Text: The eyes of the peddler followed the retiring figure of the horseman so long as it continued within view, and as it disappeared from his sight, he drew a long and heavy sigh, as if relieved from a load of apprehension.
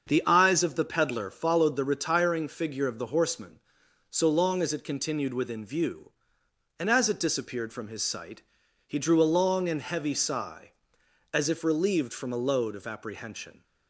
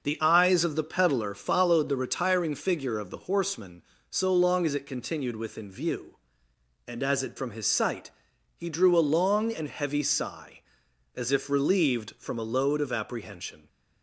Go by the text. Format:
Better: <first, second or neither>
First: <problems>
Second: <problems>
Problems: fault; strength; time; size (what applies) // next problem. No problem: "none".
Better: first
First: starts louder than the rest; until 1.1 s; 6.5 dB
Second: starts louder than the rest; noticeable; until 1.0 s; 6 dB // skips "disappeared"; at 7.3 s